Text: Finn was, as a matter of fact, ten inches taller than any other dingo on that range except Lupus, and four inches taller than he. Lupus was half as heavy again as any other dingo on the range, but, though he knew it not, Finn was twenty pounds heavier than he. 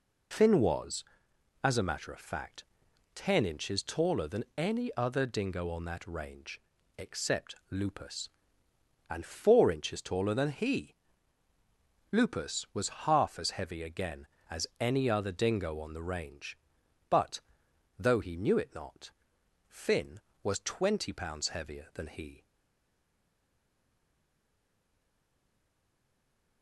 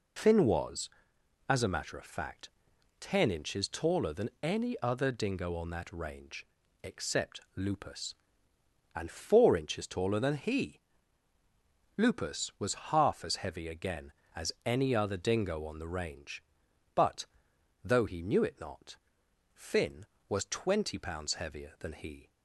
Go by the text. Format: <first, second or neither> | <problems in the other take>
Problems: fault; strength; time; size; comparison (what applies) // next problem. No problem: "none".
second | pauses between "range" and "except"; at 6.5 s; 0.40 s long; also in the second // pauses between "except" and "Lupus"; slight; at 7.5 s; 0.16 s long; slight in the second // stays silent after the last word; strong; from 22.4 s on; 4.2 s long